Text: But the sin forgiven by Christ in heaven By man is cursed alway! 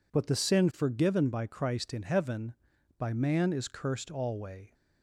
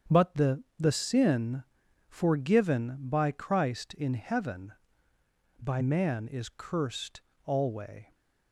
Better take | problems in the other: first | starts louder than the rest; strong; until 1.2 s; 7.5 dB // says "the" twice; at 0.7 s // pauses between "sin" and "forgiven"; at 1.6 s; 0.44 s long // pauses between "cursed" and "alway"; slight; at 7.2 s; 0.24 s long

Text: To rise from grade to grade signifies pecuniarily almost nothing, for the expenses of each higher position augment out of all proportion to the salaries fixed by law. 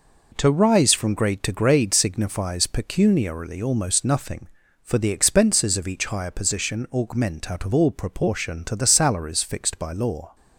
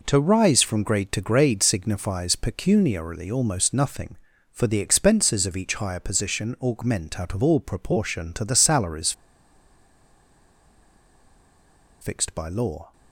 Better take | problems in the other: first | pauses between "salaries" and "fixed"; strong; at 9.1 s; 2.8 s long

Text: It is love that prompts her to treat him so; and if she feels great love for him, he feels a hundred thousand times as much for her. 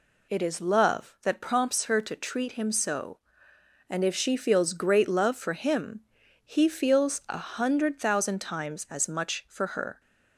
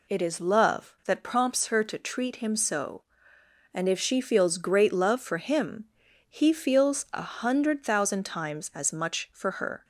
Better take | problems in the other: neither | none

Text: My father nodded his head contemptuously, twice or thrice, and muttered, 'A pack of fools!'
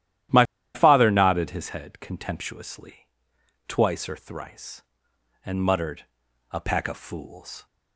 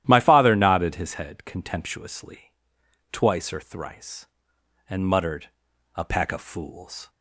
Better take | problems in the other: second | starts louder than the rest; strong; until 1.6 s; 12 dB; strong in the second // pauses between "My" and "father"; slight; at 0.4 s; 0.30 s long

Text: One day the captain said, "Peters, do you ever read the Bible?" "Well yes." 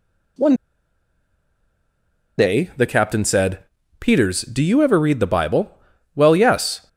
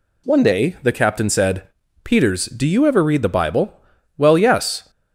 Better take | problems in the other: second | pauses between "One" and "day"; strong; at 0.5 s; 1.8 s long

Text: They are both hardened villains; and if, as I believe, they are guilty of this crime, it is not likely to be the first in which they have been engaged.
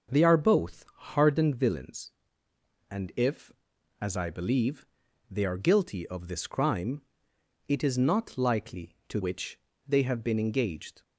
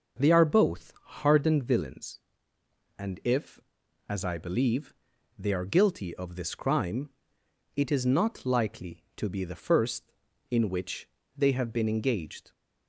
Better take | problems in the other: second | starts louder than the rest; until 1.4 s; 7 dB; also in the second // pauses between "both" and "hardened"; slight; at 0.8 s; 0.28 s long; slight in the second // skips "be the first in"; at 9.2 s // pauses between "which" and "they"; slight; at 9.5 s; 0.26 s long; slight in the second

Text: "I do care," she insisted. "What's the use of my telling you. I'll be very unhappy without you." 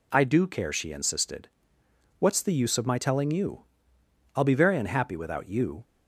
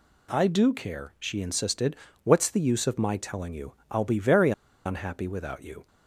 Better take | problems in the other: first | pauses between "very" and "unhappy"; slight; at 4.5 s; 0.34 s long

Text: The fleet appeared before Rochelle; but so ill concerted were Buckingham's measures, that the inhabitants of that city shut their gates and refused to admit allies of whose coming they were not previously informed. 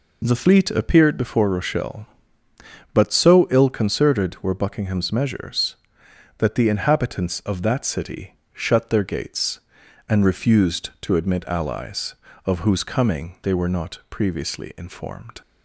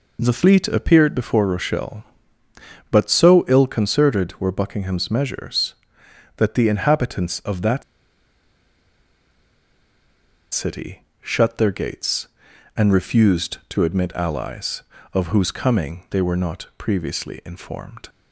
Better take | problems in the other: first | pauses between "that" and "city"; strong; at 7.8 s; 2.7 s long // pauses between "city" and "shut"; slight; at 11.0 s; 0.18 s long; slight in the first

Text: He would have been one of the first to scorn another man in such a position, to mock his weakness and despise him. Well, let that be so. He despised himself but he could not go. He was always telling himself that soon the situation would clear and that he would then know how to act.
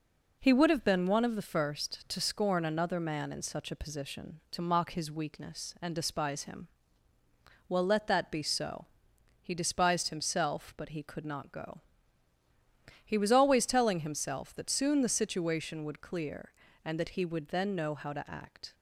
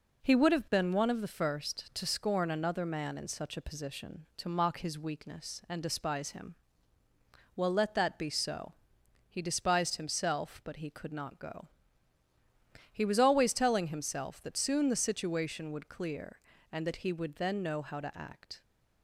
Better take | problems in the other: neither | none

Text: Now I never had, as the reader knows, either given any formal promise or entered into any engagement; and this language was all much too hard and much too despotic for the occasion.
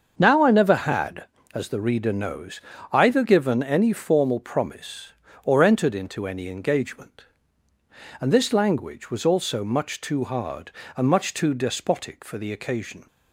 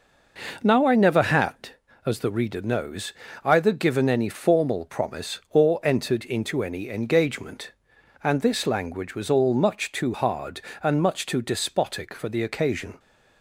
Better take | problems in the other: second | starts louder than the rest; until 1.1 s; 6.5 dB // says "also" for "all"; at 9.2 s

